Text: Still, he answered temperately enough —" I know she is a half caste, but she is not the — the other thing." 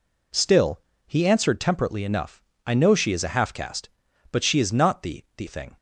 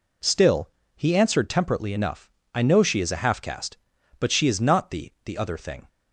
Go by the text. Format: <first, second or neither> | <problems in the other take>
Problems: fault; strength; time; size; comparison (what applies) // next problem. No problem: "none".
second | skips "other"; at 5.4 s